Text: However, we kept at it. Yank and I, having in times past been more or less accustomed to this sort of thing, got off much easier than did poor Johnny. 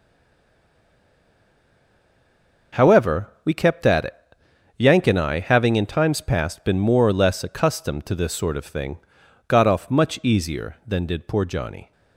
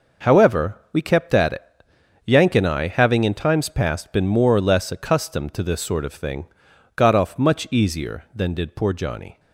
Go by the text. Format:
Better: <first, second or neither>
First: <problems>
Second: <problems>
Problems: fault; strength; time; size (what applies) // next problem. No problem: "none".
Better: second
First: stays silent before the first word; strong; until 2.7 s; 2.7 s long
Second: none